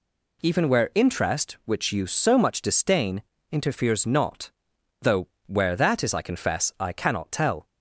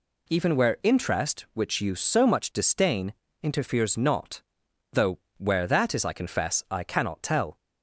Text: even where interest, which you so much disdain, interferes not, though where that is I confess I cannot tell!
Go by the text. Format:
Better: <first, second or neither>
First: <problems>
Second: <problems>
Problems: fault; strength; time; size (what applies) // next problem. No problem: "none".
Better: neither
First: pauses between "though" and "where"; slight; at 5.2 s; 0.18 s long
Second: pauses between "though" and "where"; slight; at 5.1 s; 0.18 s long